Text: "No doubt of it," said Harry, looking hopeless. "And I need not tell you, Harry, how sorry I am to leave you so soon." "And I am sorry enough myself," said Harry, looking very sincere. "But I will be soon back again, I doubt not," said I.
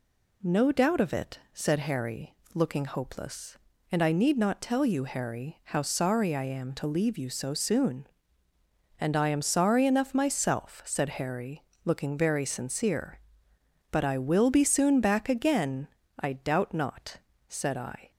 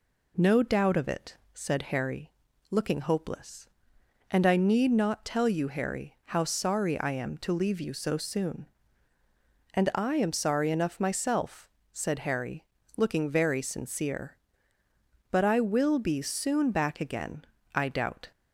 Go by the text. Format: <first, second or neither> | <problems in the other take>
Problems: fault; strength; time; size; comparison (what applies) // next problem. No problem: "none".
first | stops before "not said I"; at 18.3 s